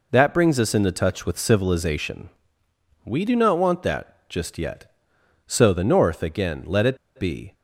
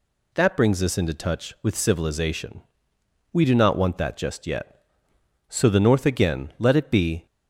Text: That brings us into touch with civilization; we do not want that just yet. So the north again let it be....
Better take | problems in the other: second | pauses between "it" and "be"; slight; at 6.9 s; 0.20 s long

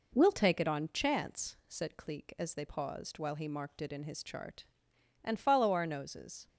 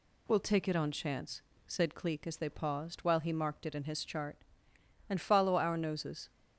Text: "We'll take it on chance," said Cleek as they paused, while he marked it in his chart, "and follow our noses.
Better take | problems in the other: neither | none

